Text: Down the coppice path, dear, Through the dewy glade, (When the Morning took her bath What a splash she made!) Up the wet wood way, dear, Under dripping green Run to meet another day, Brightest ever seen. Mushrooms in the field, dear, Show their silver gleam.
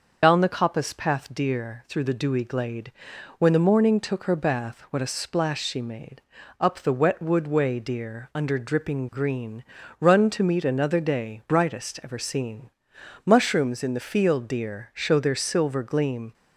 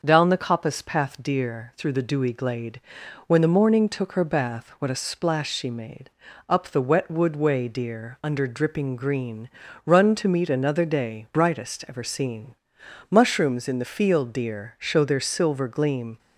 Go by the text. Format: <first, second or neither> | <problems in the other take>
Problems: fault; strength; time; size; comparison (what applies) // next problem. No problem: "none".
second | loses the start of "Down"; at 0.2 s; 75 ms // starts louder than the rest; until 1.2 s; 6 dB; also in the second // pauses between "green" and "Run"; slight; at 9.6 s; 0.36 s long; slight in the second